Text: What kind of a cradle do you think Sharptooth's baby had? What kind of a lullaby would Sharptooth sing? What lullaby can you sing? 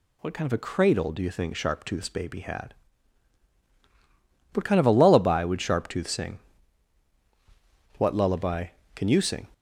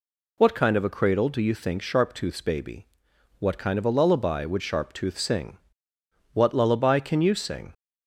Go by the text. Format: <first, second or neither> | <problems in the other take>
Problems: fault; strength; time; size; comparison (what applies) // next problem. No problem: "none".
first | skips "had"; at 3.1 s